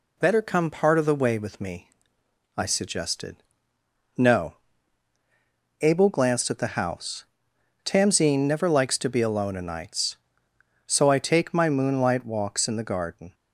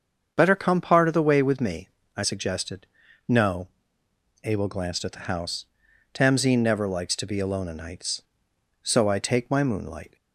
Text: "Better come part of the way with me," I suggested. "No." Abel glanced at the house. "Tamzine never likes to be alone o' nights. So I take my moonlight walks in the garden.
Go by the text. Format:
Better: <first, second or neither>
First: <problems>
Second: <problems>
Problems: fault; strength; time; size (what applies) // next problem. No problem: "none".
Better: first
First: none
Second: starts louder than the rest; until 1.3 s; 7 dB // stops before "walks in the garden"; at 10.1 s